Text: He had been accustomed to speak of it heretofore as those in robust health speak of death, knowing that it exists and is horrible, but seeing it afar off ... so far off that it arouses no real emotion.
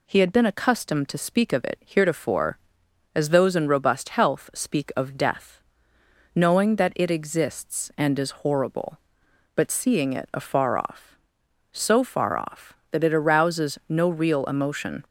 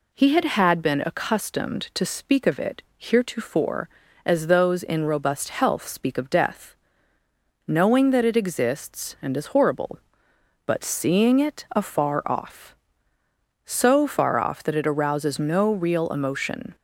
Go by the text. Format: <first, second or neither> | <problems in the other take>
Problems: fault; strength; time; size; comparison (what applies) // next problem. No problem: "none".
first | says "had" twice; at 0.4 s